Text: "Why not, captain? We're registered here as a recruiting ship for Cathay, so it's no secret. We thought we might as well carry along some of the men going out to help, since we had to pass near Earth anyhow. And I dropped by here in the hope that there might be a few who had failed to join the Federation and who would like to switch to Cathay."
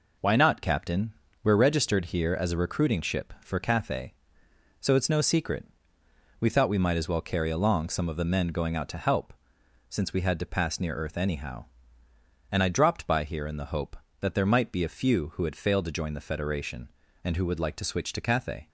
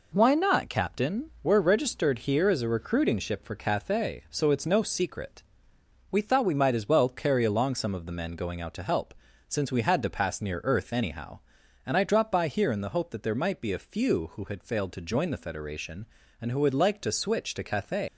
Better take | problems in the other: first | leaves "Cathay" unfinished; at 18.0 s; 130 ms

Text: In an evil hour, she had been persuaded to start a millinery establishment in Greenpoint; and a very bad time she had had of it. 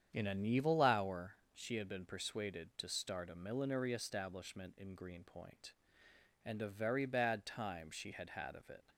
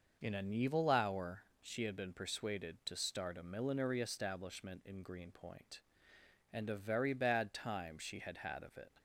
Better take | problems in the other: second | starts louder than the rest; strong; until 1.1 s; 8.5 dB

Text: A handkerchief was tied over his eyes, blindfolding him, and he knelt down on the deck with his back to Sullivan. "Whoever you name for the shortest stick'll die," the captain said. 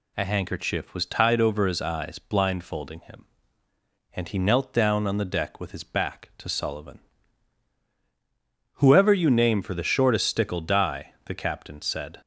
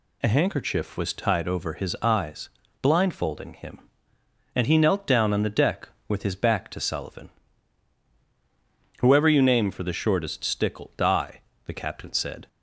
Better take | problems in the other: neither | none

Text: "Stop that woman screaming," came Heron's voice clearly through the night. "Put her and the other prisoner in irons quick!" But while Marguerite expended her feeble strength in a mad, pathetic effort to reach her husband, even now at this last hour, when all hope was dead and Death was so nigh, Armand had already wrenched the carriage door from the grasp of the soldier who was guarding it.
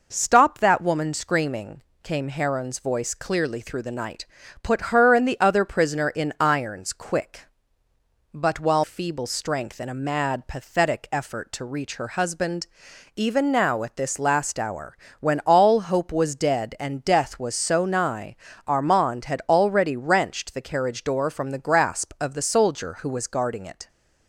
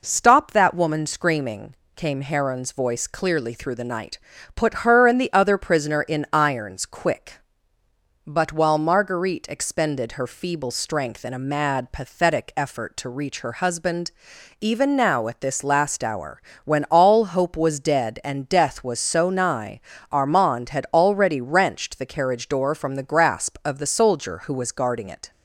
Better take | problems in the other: second | skips "Marguerite expended her"; at 8.8 s

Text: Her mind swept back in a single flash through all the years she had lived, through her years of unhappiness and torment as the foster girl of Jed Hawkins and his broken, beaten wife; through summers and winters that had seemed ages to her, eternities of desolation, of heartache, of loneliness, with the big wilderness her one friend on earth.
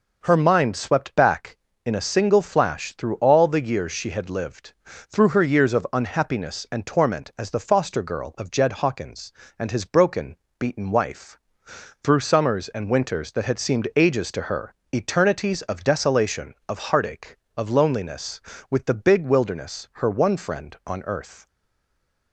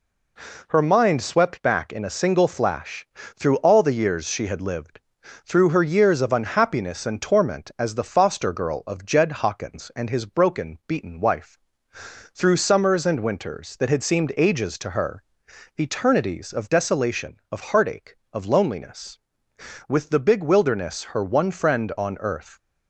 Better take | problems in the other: second | stays silent after the last word; slight; from 21.4 s on; 0.9 s long

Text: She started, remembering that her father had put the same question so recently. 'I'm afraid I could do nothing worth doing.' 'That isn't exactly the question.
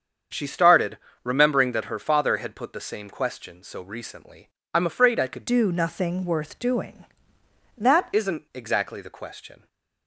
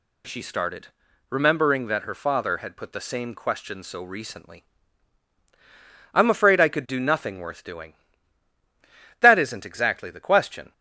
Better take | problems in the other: second | starts louder than the rest; strong; until 1.6 s; 7.5 dB // changes voice from "do" to "That"; from 5.4 to 8.0 s; 2.6 s long

